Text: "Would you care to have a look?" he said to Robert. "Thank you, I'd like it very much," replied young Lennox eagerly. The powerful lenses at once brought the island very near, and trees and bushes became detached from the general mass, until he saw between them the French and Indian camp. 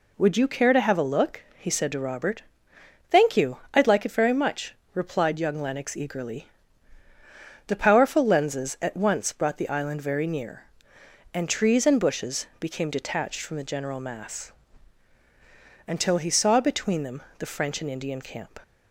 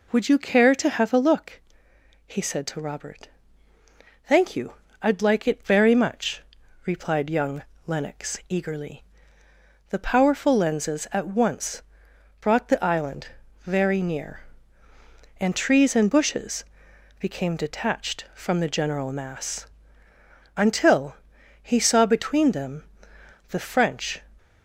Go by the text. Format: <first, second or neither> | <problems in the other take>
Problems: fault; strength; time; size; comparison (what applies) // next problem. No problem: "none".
first | pauses between "young" and "Lennox"; slight; at 7.6 s; 0.24 s long // pauses between "once" and "brought"; noticeable; at 11.8 s; 0.58 s long // pauses between "island" and "very"; at 13.2 s; 0.40 s long // pauses between "bushes" and "became"; noticeable; at 16.6 s; 0.54 s long // pauses between "until" and "he"; noticeable; at 21.1 s; 0.46 s long // pauses between "them" and "the"; noticeable; at 22.8 s; 0.66 s long; slight in the first // stops before "and Indian camp"; at 24.3 s